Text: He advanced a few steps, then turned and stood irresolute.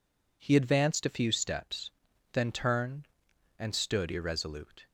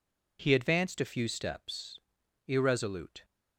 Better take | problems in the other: first | skips "then turned and stood"; at 2.2 s

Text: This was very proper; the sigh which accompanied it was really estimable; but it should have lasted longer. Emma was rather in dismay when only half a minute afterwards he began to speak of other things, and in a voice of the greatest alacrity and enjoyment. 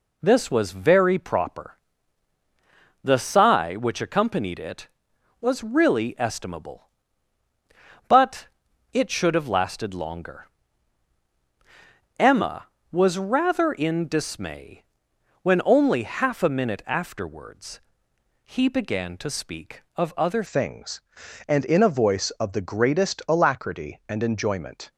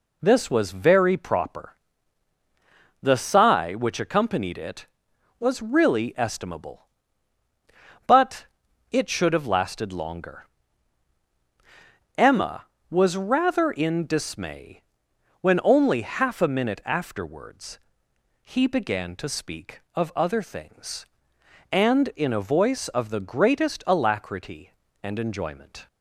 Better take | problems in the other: second | pauses between "but" and "it"; at 8.4 s; 0.44 s long; also in the second // pauses between "dismay" and "when"; noticeable; at 14.8 s; 0.56 s long; noticeable in the second // pauses between "afterwards" and "he"; noticeable; at 17.8 s; 0.64 s long; noticeable in the second // changes voice at "things"; from 20.4 s on; 4.5 s long

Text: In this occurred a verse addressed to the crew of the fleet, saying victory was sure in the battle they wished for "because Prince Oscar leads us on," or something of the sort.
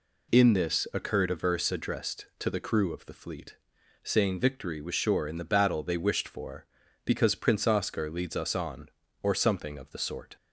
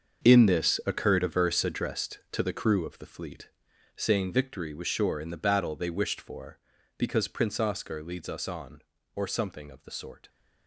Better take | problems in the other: first | gets quieter; strong; throughout; 13 dB

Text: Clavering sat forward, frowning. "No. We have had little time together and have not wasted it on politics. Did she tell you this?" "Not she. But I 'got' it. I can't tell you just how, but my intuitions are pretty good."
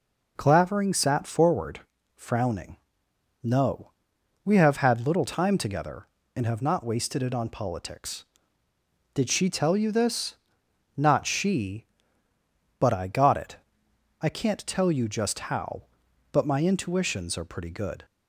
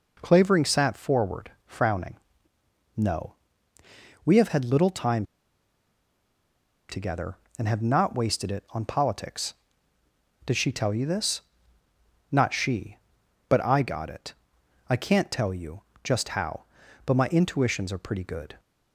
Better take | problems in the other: first | pauses between "time" and "together"; strong; at 5.2 s; 1.6 s long // pauses between "you" and "just"; slight; at 15.8 s; 0.22 s long

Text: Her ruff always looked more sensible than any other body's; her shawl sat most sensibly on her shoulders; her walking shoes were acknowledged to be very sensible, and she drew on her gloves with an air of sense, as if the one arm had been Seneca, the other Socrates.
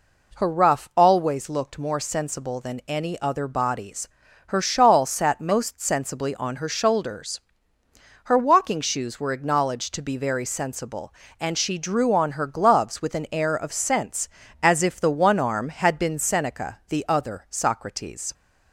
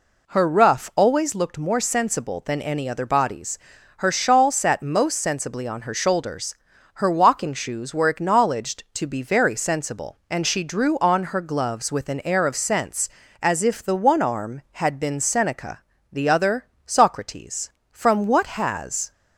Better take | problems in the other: first | goes on to say "From what has"; noticeable; from 17.9 s on; 1.2 s long

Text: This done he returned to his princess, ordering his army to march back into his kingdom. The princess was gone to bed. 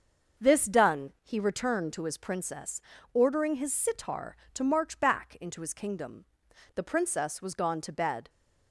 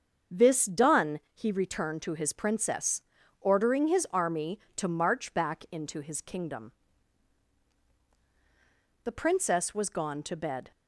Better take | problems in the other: second | starts louder than the rest; until 1.5 s; 6.5 dB; also in the second // says "sitar" for "army"; at 3.7 s

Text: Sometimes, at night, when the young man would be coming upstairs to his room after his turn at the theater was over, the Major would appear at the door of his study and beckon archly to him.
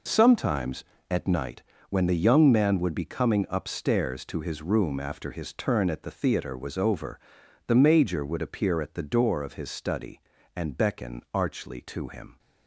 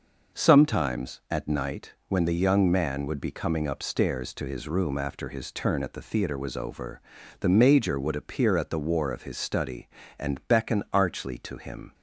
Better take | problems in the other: first | says "war" for "door"; at 8.7 s

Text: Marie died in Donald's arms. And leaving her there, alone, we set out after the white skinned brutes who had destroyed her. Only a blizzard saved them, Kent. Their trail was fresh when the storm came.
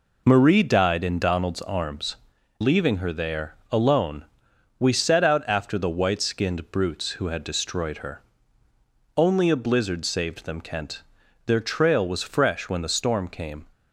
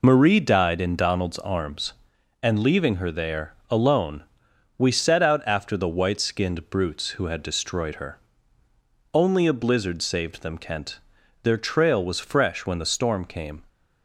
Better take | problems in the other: second | skips "And"; at 2.3 s

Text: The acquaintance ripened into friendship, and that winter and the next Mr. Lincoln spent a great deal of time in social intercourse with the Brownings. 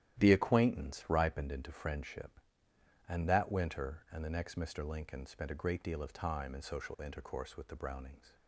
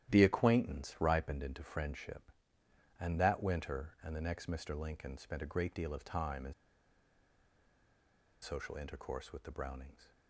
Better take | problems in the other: first | starts louder than the rest; strong; until 1.1 s; 12 dB; strong in the first // pauses between "in" and "social"; strong; at 6.5 s; 1.8 s long

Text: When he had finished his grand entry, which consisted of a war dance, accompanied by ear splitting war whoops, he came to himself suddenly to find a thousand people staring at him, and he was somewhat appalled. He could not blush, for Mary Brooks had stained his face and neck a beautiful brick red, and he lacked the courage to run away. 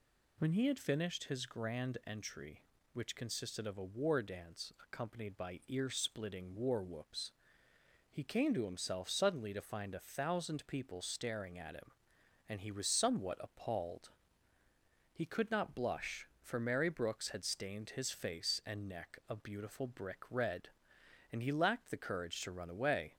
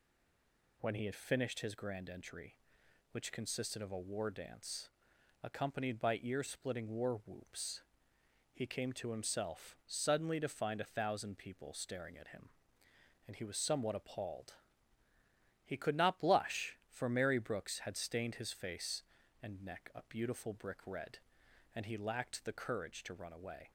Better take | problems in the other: first | stays silent before the first word; slight; until 0.8 s; 0.8 s long

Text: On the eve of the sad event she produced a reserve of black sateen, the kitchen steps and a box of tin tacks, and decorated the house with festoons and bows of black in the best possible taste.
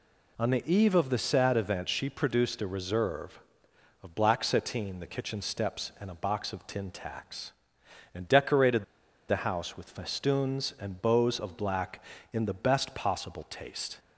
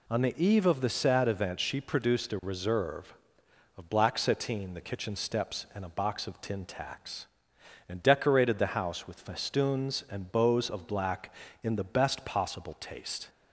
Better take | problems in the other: second | pauses between "decorated" and "the"; at 8.8 s; 0.45 s long

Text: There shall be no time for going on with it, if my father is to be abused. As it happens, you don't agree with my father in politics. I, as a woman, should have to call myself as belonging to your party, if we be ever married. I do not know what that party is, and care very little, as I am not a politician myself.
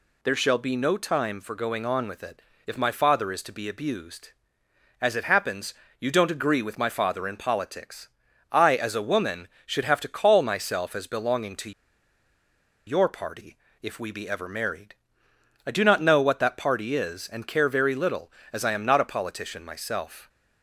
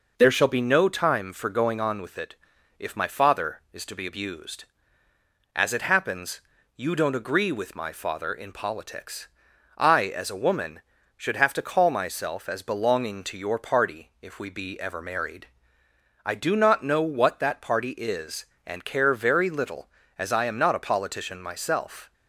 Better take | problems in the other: second | pauses between "to" and "your"; at 11.7 s; 1.1 s long

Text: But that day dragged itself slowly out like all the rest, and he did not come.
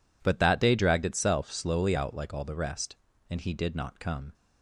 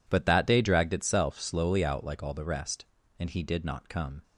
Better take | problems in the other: neither | none

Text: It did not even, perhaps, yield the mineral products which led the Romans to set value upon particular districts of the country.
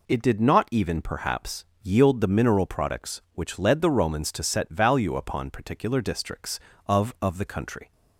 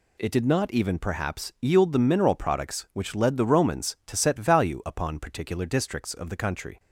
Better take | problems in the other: second | says "of" twice; at 7.2 s

